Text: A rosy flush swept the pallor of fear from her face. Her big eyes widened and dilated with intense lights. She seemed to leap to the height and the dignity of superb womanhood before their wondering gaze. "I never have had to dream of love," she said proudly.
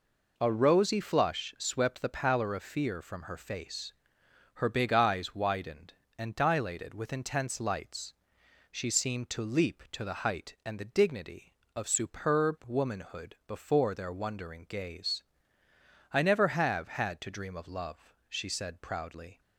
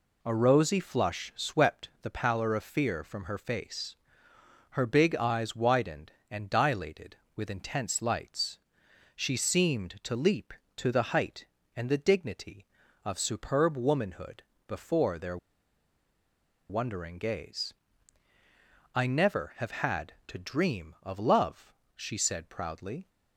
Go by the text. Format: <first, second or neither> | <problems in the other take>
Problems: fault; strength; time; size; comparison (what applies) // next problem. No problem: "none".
first | pauses between "womanhood" and "before"; slight; at 14.4 s; 0.24 s long // pauses between "their" and "wondering"; strong; at 15.3 s; 1.3 s long